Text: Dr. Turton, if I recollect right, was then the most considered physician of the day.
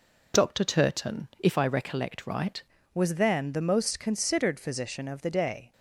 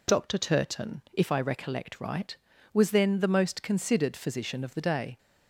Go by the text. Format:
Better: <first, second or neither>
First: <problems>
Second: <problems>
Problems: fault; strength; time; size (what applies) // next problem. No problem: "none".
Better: second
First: changes voice at "was"; from 2.9 s on; 2.8 s long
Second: none